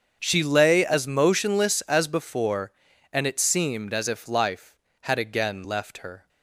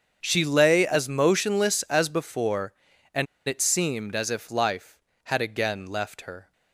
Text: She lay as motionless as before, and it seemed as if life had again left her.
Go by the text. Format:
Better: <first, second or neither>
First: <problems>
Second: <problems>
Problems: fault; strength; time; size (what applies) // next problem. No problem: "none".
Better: first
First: starts louder than the rest; until 1.2 s; 7 dB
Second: starts louder than the rest; strong; until 1.2 s; 7 dB // pauses between "and" and "it"; slight; at 3.2 s; 0.22 s long